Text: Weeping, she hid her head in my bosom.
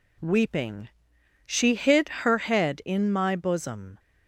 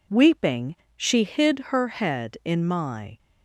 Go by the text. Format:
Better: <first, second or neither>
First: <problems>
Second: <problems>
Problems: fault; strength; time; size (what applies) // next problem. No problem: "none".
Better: first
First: none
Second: stops before "bosom"; at 3.1 s